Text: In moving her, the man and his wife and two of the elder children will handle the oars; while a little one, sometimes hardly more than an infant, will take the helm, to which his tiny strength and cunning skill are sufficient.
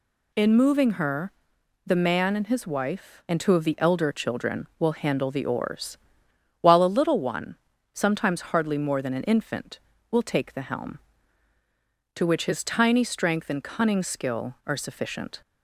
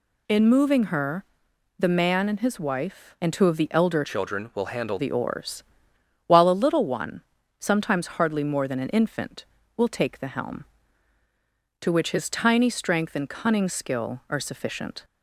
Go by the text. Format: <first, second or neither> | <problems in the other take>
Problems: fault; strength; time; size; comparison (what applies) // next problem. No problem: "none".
first | changes voice from "children" to "handle"; from 4.0 to 4.9 s; 0.9 s long